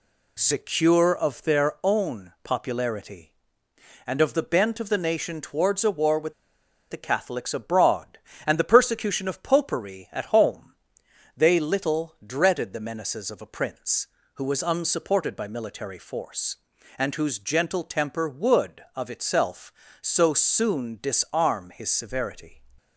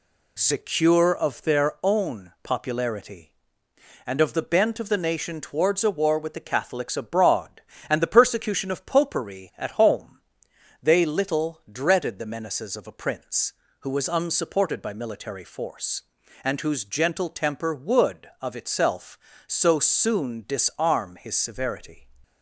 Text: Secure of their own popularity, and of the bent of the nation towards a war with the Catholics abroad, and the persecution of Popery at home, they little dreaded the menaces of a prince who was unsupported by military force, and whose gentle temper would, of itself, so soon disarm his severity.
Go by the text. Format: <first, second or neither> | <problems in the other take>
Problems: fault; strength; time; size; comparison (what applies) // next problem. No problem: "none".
second | pauses between "with" and "the"; noticeable; at 6.3 s; 0.56 s long